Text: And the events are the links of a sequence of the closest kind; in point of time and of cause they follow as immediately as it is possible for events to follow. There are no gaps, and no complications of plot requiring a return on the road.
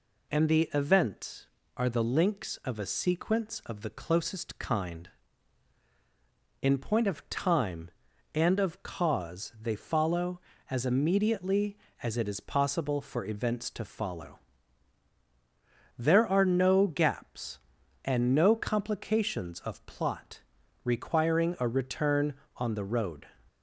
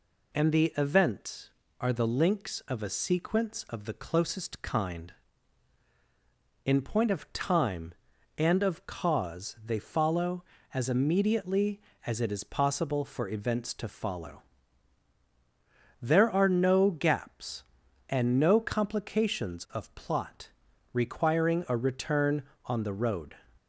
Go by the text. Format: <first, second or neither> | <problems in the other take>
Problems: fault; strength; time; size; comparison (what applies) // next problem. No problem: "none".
neither | pauses between "plot" and "requiring"; the same in both